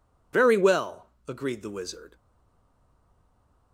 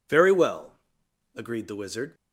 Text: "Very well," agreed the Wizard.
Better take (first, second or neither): second